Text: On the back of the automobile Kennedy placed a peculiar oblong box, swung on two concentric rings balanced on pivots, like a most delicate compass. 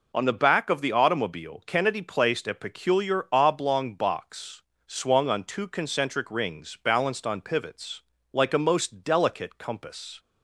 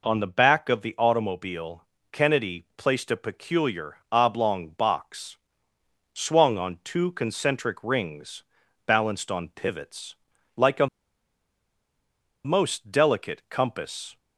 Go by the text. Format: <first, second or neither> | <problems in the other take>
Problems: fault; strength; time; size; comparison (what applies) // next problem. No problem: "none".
first | pauses between "automobile" and "Kennedy"; slight; at 1.8 s; 0.28 s long // pauses between "peculiar" and "oblong"; slight; at 3.9 s; 0.16 s long // pauses between "rings" and "balanced"; at 8.4 s; 0.42 s long // pauses between "a" and "most"; strong; at 10.8 s; 1.5 s long